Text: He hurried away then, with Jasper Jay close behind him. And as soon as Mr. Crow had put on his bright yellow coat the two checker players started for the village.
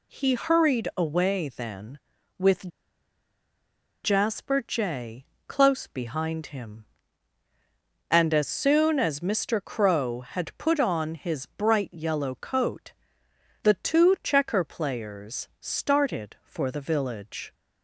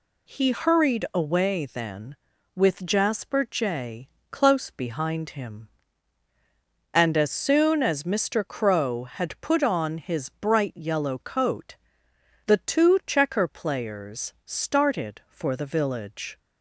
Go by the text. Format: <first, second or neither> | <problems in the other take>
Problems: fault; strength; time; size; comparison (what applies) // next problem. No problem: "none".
second | pauses between "with" and "Jasper"; strong; at 2.6 s; 1.3 s long // pauses between "Jay" and "close"; slight; at 5.2 s; 0.24 s long; slight in the second // pauses between "coat" and "the"; noticeable; at 12.9 s; 0.70 s long; noticeable in the second